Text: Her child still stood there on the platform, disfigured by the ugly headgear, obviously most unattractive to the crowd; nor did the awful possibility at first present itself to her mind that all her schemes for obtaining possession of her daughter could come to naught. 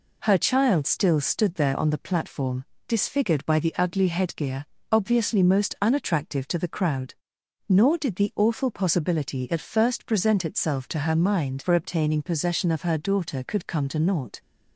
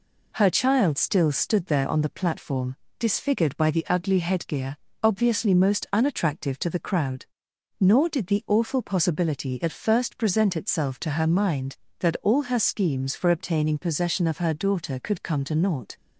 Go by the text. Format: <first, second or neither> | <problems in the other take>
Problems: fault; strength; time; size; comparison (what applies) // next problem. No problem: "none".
second | skips "that all her schemes"; at 11.6 s